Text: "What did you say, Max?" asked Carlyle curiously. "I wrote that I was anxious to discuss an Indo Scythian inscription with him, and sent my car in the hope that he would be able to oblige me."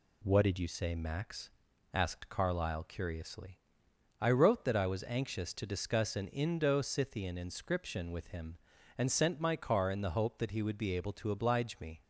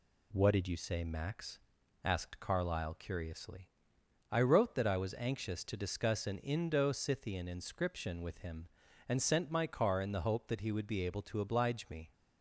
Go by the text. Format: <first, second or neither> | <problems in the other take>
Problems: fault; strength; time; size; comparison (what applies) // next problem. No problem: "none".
neither | none